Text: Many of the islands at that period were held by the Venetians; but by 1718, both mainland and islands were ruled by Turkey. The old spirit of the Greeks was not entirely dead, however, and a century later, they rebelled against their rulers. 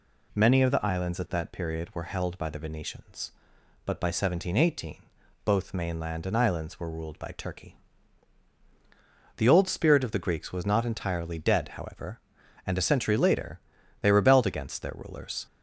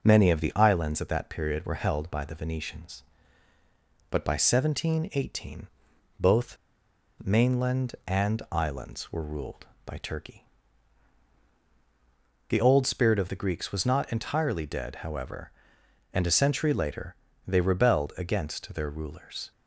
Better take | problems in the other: first | pauses between "both" and "mainland"; noticeable; at 6.5 s; 0.69 s long

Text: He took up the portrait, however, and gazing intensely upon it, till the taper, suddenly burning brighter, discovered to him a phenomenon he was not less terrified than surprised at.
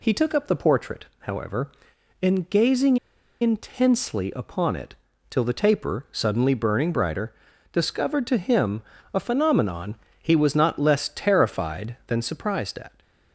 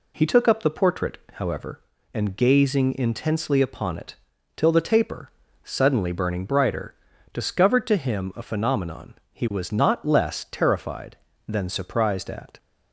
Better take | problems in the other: second | pauses between "gazing" and "intensely"; at 2.9 s; 0.45 s long // pauses between "him" and "a"; slight; at 8.8 s; 0.28 s long // pauses between "phenomenon" and "he"; slight; at 9.9 s; 0.26 s long; slight in the second

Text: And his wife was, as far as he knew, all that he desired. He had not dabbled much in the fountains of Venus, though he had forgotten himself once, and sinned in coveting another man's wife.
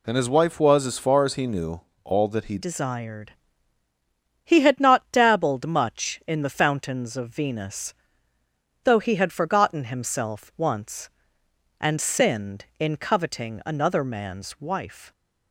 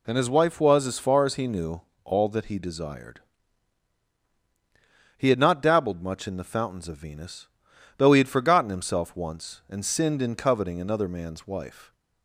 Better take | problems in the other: second | changes voice at "desired"; from 2.5 s on; 12.6 s long

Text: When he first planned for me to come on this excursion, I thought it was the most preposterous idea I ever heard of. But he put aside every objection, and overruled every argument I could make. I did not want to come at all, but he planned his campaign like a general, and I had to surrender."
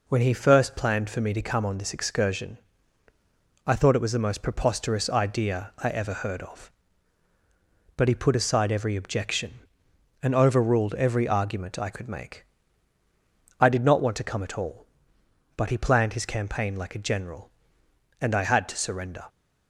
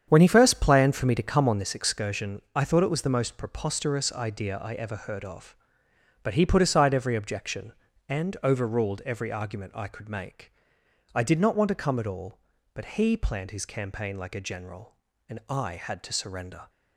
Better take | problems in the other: first | starts louder than the rest; strong; until 1.7 s; 8 dB

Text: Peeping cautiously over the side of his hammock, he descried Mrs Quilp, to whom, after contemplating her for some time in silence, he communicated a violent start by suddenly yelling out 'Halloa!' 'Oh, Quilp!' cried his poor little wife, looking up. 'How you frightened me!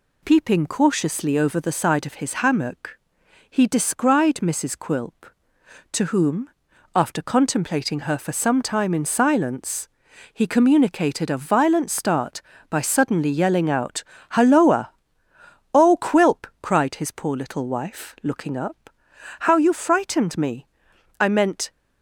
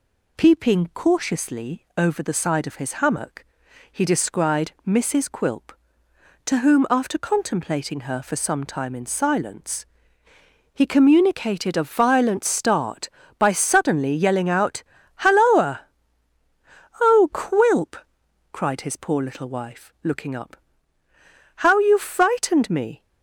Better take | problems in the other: second | pauses between "out" and "Halloa"; slight; at 14.0 s; 0.28 s long; slight in the second // goes on to say "I meant"; from 21.1 s on; 0.50 s long

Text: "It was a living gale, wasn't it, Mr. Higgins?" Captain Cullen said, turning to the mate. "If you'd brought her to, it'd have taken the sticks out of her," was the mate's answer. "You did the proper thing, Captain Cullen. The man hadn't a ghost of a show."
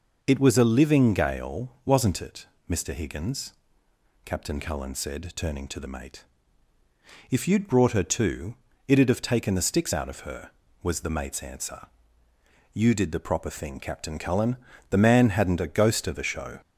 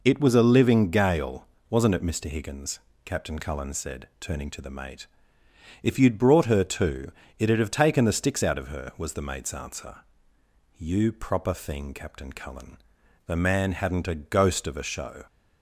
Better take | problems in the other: first | skips "did the"; at 11.1 s

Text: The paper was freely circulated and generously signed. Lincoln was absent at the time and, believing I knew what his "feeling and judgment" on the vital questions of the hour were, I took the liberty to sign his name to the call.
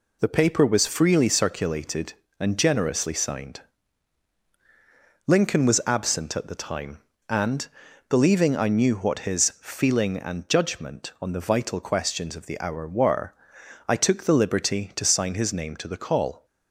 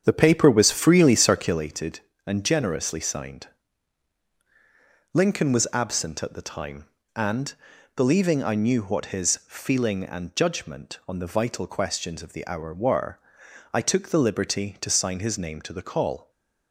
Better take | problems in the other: first | starts louder than the rest; strong; until 1.7 s; 8 dB // stays silent after the last word; slight; from 16.2 s on; 0.5 s long

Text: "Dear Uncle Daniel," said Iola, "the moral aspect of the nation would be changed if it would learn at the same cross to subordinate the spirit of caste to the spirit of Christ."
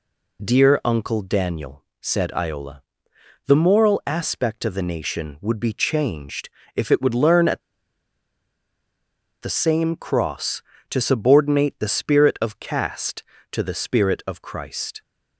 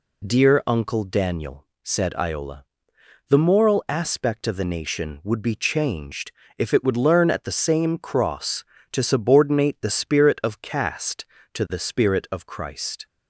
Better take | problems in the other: second | pauses between "changed" and "if"; slight; at 6.4 s; 0.26 s long; slight in the second // pauses between "at" and "the"; strong; at 7.6 s; 1.8 s long

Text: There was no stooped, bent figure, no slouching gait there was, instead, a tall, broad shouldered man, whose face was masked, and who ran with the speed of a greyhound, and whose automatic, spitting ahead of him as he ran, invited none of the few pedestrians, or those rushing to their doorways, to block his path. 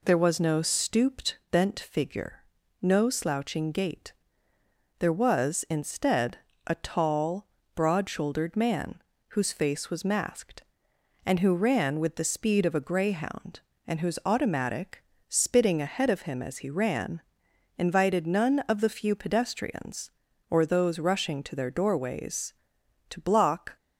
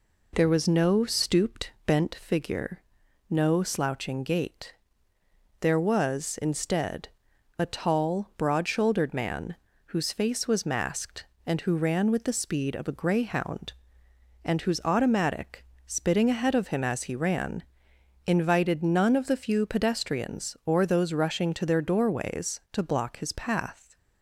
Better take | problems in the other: second | pauses between "gait" and "there"; noticeable; at 4.1 s; 0.88 s long; noticeable in the second // stops before "his path"; at 23.7 s

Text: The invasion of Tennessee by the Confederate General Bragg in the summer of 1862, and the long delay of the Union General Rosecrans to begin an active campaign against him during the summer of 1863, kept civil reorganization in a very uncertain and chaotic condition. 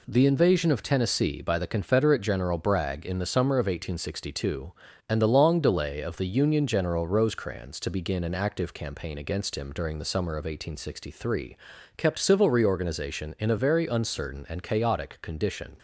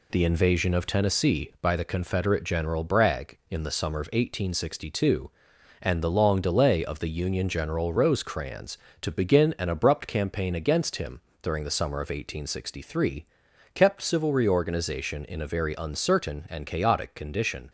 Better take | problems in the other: first | says "abrupt" for "active"; at 9.6 s // pauses between "him" and "during"; slight; at 11.2 s; 0.22 s long

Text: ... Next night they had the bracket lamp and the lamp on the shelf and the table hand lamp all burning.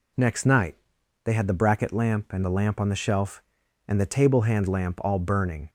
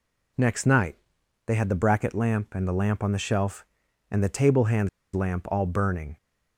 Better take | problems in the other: first | pauses between "night" and "they"; noticeable; at 0.9 s; 0.50 s long; noticeable in the first // pauses between "hand" and "lamp"; slight; at 4.8 s; 0.25 s long

